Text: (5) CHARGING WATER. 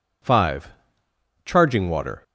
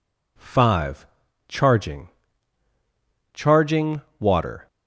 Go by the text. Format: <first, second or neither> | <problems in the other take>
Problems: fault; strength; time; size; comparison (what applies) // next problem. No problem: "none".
first | says "CHARGING" twice; at 3.3 s